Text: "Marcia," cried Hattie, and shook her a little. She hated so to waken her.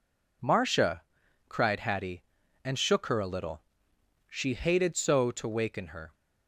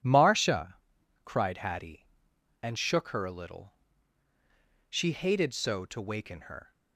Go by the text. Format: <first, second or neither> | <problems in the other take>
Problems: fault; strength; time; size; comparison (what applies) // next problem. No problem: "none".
neither | none